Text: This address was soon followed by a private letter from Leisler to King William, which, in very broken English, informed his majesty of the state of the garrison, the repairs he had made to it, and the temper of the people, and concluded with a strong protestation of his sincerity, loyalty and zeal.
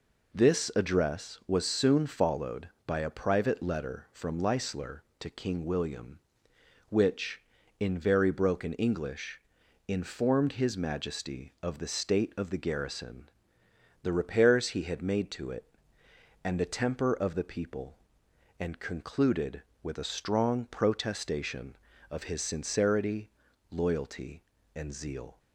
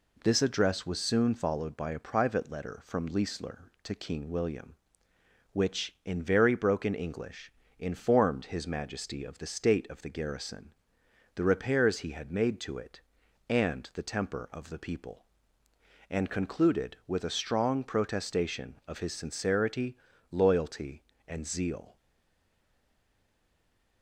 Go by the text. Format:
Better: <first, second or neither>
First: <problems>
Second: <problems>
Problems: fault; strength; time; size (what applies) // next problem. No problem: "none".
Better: first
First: none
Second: stays silent after the last word; noticeable; from 21.9 s on; 2.1 s long